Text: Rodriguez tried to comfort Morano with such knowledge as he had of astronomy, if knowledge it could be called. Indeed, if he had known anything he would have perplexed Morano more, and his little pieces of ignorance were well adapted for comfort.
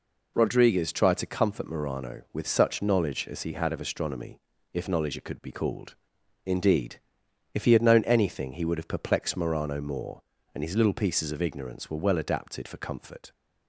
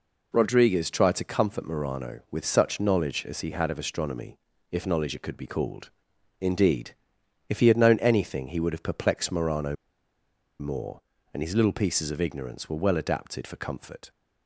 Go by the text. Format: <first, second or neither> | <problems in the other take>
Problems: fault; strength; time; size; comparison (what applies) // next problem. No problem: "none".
first | pauses between "Morano" and "more"; noticeable; at 9.7 s; 0.84 s long